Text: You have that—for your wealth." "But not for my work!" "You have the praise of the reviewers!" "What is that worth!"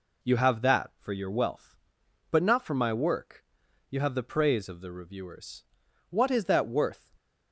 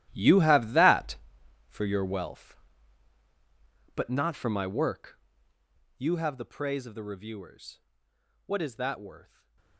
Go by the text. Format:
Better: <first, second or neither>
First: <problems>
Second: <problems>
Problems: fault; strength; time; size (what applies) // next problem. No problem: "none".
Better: first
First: none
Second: gets quieter; strong; throughout; 15 dB // stays silent after the last word; slight; from 9.2 s on; 0.5 s long